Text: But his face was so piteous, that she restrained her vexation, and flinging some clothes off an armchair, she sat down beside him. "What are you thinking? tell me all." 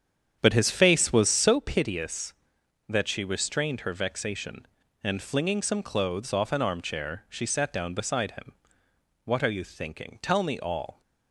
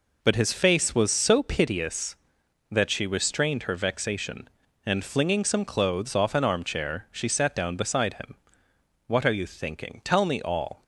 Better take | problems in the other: second | starts louder than the rest; strong; until 1.6 s; 8.5 dB

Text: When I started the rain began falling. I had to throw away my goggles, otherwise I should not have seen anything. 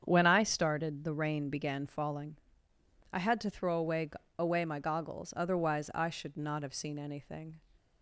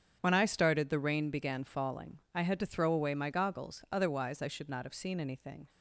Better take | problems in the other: second | starts louder than the rest; strong; until 1.0 s; 8 dB; strong in the second // says "away" twice; at 4.3 s

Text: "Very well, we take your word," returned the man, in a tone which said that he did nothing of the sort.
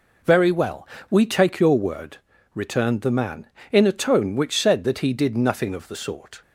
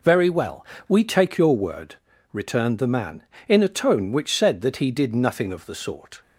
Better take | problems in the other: neither | none

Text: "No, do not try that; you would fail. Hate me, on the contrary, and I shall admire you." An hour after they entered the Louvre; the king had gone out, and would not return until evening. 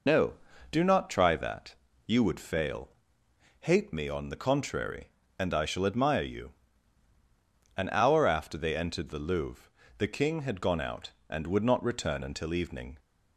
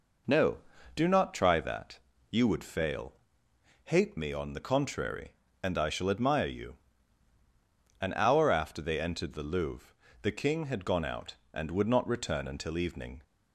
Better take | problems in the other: second | loses the start of "No"; at 0.0 s; 35 ms

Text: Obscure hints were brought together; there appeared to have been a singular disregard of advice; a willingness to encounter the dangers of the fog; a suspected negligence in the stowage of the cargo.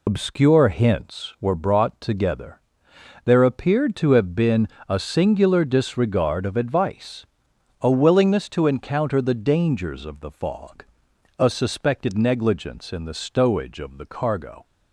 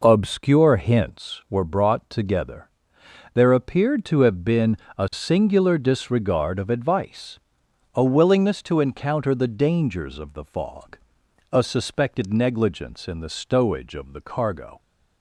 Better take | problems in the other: second | loses the start of "Obscure"; at 0.0 s; 135 ms // pauses between "been" and "a"; slight; at 4.6 s; 0.22 s long; slight in the second

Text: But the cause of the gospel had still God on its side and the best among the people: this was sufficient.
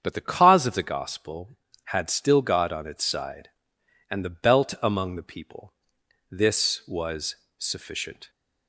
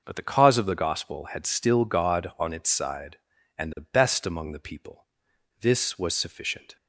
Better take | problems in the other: second | starts louder than the rest; strong; until 1.0 s; 7.5 dB // says "belt" for "best"; at 4.2 s // pauses between "was" and "sufficient"; slight; at 7.3 s; 0.24 s long

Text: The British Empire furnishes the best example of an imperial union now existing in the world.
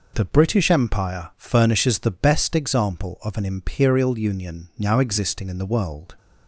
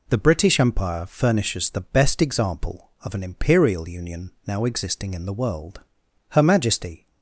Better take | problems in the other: first | goes on to say "Her Majesty"; noticeable; from 6.3 s on; 0.76 s long

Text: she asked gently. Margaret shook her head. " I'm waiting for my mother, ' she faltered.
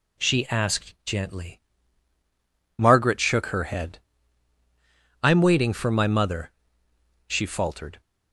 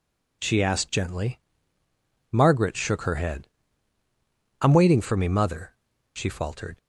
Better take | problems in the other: first | says "me" for "my"; at 5.1 s

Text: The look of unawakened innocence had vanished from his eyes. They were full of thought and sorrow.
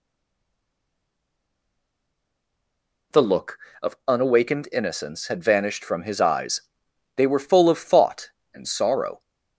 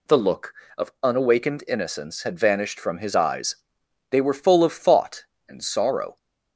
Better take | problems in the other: second | stays silent before the first word; strong; until 3.1 s; 3.1 s long

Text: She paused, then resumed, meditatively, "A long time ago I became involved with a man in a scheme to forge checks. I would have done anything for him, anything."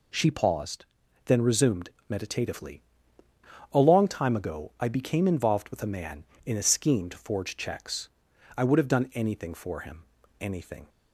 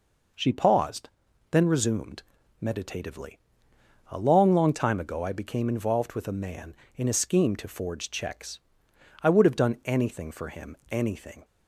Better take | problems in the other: first | says "long" twice; at 4.5 s

